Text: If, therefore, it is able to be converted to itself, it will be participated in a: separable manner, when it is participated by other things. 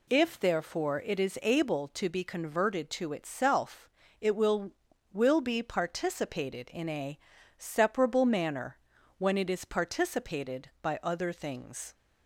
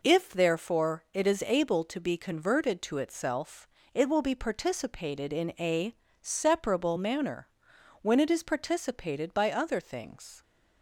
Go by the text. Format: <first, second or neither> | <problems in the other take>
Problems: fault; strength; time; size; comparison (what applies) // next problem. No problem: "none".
second | says "will" twice; at 5.1 s